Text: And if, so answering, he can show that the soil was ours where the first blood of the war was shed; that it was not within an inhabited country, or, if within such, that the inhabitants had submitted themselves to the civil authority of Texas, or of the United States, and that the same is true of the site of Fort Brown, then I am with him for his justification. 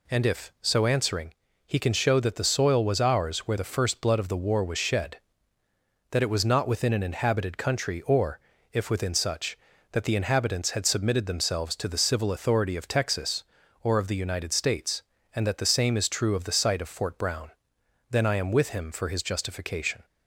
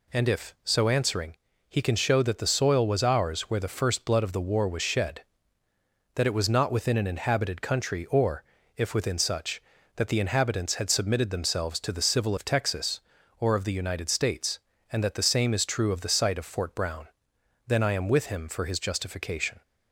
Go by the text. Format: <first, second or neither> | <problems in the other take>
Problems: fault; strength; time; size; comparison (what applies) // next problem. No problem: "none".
first | skips "authority"; at 12.3 s